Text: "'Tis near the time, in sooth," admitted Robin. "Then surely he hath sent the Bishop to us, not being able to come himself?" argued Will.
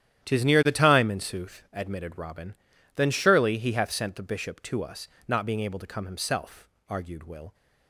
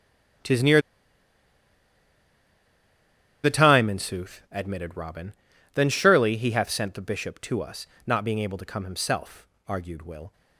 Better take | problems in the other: first | starts louder than the rest; strong; until 4.0 s; 11 dB; strong in the first // pauses between "near" and "the"; strong; at 0.7 s; 2.6 s long

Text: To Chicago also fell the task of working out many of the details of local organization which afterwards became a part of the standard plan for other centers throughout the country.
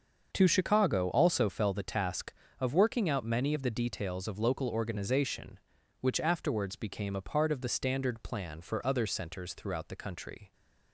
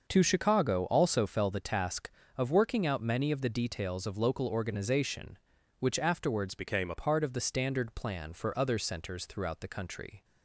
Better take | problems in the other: first | starts louder than the rest; noticeable; until 1.0 s; 6 dB; also in the first // changes voice from "became" to "a"; from 6.5 to 6.9 s; 0.4 s long

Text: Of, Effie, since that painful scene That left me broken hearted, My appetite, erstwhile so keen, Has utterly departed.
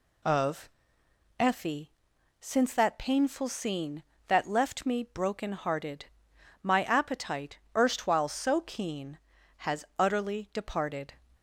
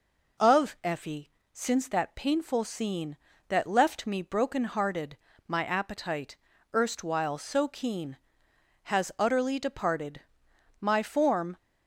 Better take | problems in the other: first | goes on to say "My form"; noticeable; from 10.7 s on; 0.78 s long

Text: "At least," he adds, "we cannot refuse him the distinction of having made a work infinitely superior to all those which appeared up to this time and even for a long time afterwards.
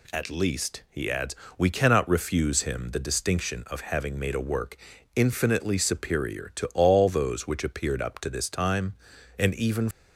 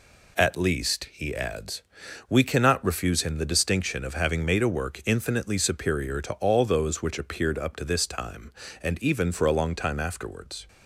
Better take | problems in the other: second | pauses between "work" and "infinitely"; at 4.7 s; 0.40 s long // stops before "for a long time afterwards"; at 9.9 s

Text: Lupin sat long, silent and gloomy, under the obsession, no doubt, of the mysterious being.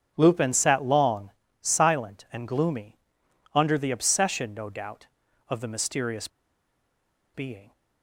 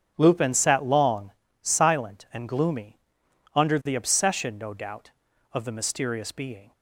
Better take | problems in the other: second | starts louder than the rest; strong; until 1.1 s; 7.5 dB; strong in the second // pauses between "mysterious" and "being"; at 6.2 s; 1.0 s long

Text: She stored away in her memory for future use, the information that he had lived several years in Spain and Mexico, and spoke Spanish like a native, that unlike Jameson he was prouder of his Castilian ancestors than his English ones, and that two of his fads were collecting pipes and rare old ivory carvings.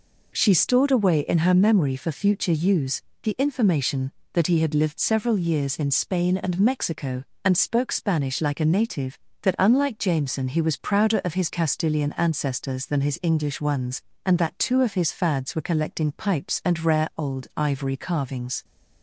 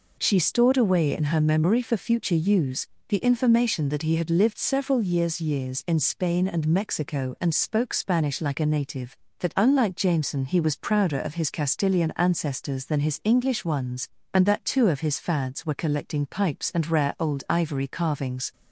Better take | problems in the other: first | says "years" twice; at 5.3 s

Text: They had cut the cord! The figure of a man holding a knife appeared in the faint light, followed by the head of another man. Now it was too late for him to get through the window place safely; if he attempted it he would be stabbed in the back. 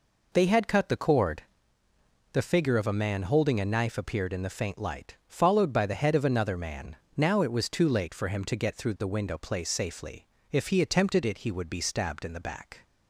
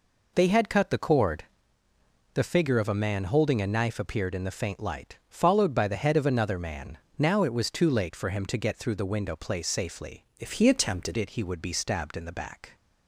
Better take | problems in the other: first | changes voice from "if" to "attempted"; from 10.3 to 11.1 s; 0.8 s long

